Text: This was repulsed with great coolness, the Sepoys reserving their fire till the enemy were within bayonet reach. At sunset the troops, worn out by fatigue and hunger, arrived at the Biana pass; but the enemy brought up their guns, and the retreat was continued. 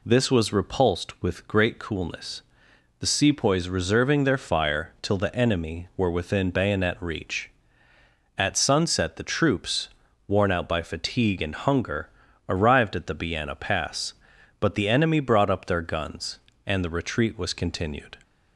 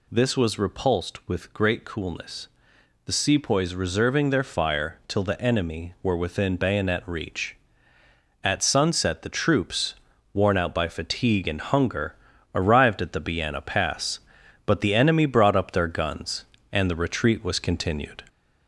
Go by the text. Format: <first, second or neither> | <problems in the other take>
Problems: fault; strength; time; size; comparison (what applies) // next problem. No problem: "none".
first | gets louder; slight; throughout; 2.5 dB